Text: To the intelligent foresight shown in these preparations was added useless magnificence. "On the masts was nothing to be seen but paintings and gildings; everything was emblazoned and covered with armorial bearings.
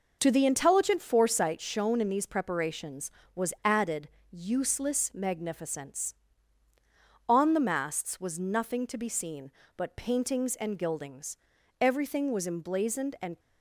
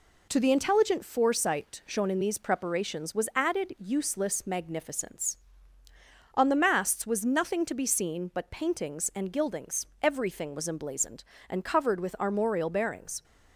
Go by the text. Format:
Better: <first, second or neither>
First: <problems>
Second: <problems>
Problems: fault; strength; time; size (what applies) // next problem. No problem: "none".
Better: second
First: pauses between "added" and "useless"; slight; at 4.0 s; 0.22 s long // stops before "covered with armorial bearings"; at 13.3 s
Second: none